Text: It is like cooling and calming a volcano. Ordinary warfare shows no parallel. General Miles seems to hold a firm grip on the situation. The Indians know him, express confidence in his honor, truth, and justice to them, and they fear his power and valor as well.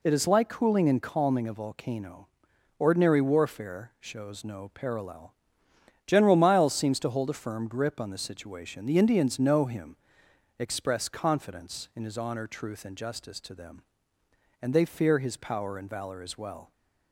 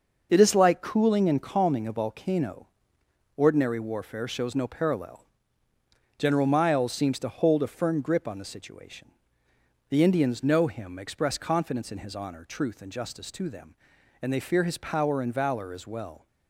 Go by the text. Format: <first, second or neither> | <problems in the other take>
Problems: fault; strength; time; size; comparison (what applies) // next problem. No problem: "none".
neither | none